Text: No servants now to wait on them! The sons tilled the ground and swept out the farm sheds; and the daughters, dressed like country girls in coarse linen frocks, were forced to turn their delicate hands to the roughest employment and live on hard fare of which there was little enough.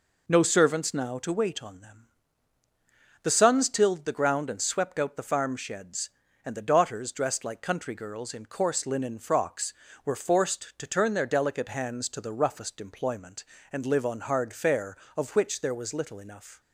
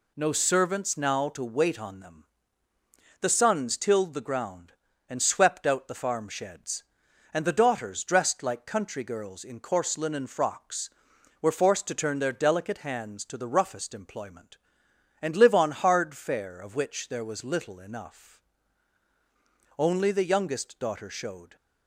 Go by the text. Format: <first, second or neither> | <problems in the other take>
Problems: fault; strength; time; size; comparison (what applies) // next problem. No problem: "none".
first | goes on to say "Only the youngest daughter showed"; strong; from 19.7 s on; 1.7 s long